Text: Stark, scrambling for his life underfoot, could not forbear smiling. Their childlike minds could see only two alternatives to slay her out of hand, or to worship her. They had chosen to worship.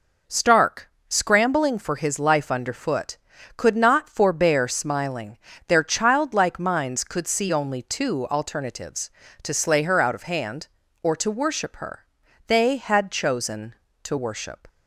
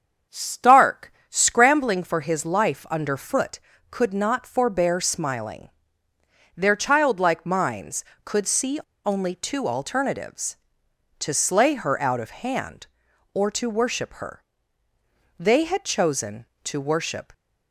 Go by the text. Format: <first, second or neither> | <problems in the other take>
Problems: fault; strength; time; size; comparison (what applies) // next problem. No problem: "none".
first | starts louder than the rest; strong; until 1.5 s; 7.5 dB // pauses between "see" and "only"; slight; at 8.7 s; 0.26 s long